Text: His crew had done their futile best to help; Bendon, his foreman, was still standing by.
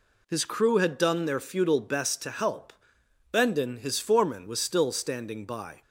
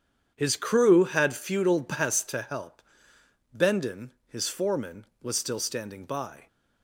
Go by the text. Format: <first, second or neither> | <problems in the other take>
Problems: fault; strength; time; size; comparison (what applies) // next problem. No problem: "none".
first | starts louder than the rest; strong; until 1.3 s; 8.5 dB // skips "done their"; at 1.3 s